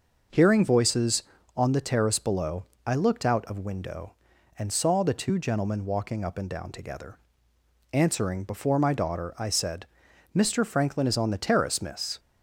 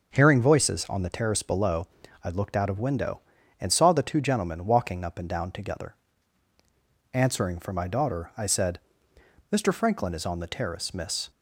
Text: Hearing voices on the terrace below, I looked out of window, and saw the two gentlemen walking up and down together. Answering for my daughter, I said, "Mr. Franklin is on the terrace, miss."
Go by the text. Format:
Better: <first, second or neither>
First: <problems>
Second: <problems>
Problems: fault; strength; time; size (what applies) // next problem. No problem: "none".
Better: second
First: starts louder than the rest; noticeable; until 1.6 s; 6 dB // says "before" for "for"; at 8.4 s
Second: starts louder than the rest; noticeable; until 1.1 s; 6 dB